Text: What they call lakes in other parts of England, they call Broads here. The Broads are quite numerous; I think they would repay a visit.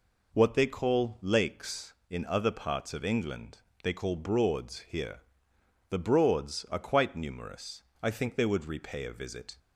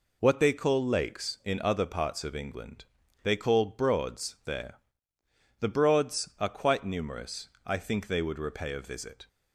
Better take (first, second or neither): first